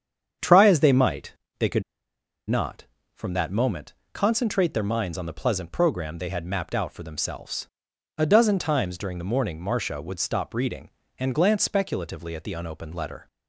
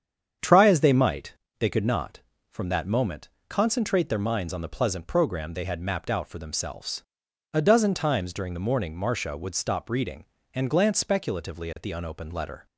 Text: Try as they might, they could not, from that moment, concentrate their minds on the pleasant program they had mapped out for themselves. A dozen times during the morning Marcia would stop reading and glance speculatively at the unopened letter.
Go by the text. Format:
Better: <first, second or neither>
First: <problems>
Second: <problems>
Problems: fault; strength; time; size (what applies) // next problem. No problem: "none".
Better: second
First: starts louder than the rest; strong; until 1.6 s; 8 dB // pauses between "could" and "not"; noticeable; at 1.8 s; 0.66 s long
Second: starts louder than the rest; strong; until 1.6 s; 8 dB